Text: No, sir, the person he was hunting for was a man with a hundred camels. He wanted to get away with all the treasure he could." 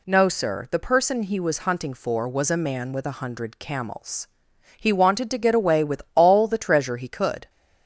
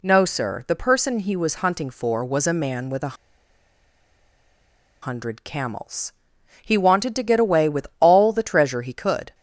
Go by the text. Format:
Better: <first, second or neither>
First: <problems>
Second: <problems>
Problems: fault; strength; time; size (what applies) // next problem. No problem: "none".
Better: first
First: none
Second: pauses between "a" and "hundred"; strong; at 3.1 s; 1.8 s long